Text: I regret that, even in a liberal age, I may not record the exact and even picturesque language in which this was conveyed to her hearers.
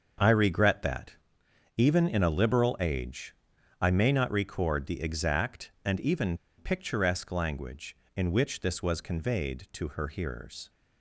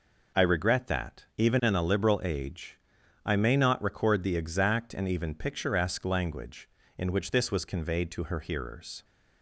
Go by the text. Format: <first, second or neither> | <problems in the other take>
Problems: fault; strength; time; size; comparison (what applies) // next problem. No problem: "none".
second | starts louder than the rest; until 1.8 s; 7 dB // pauses between "even" and "picturesque"; slight; at 6.3 s; 0.22 s long